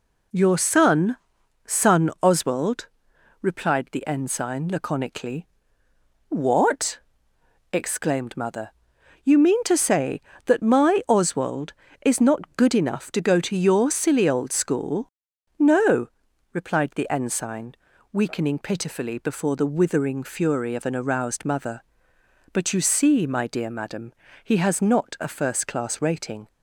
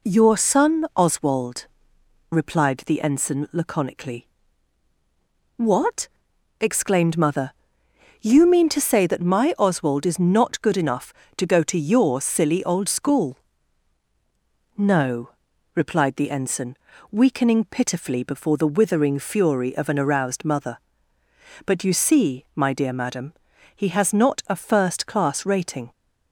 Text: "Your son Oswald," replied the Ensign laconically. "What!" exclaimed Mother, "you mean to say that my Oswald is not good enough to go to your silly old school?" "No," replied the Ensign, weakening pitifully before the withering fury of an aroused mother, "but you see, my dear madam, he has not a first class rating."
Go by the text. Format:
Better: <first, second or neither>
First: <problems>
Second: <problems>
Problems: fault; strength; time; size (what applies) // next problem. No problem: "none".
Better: second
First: says "son" twice; at 1.6 s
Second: none